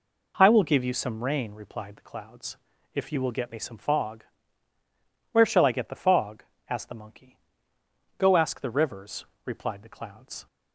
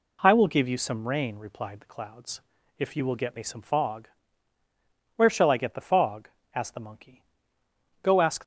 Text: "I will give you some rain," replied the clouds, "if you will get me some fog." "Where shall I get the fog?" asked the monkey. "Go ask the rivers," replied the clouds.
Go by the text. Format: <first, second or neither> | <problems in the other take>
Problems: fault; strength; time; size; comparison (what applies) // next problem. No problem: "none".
first | stops before "the rivers replied the clouds"; at 8.4 s